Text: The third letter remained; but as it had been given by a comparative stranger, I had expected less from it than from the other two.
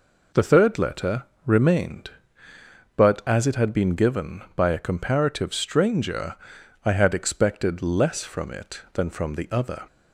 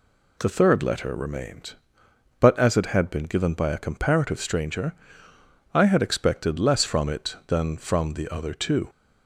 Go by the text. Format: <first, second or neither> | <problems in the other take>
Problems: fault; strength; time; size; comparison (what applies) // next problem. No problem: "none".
second | pauses between "letter" and "remained"; slight; at 1.2 s; 0.20 s long // stops before "two"; at 9.8 s